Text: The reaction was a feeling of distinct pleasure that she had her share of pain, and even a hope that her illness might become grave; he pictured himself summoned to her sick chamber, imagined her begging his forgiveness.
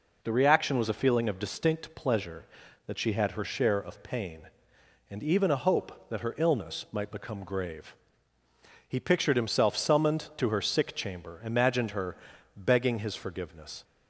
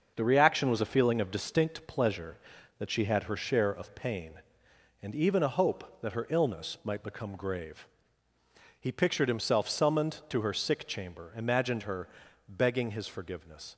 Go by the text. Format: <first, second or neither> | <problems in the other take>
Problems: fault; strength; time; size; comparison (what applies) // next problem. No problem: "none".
first | gets quieter; throughout; 6 dB // pauses between "her" and "begging"; at 12.0 s; 0.40 s long; also in the first